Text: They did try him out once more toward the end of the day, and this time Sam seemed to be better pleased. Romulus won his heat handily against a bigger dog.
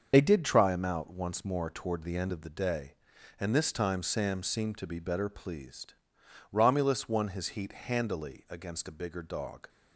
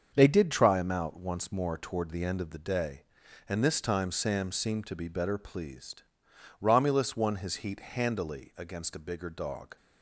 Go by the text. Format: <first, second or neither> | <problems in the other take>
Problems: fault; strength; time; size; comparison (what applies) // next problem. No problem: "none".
second | loses the start of "They"; at 0.1 s; 55 ms // starts louder than the rest; until 1.1 s; 6.5 dB; also in the second